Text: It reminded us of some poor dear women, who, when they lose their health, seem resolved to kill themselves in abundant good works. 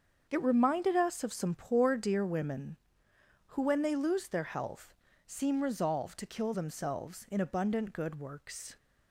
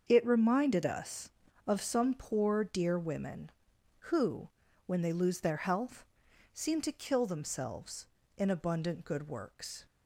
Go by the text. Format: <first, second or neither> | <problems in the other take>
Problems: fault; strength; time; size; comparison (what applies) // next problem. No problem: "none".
first | starts louder than the rest; until 1.0 s; 6.5 dB; also in the first // skips "resolved"; at 6.8 s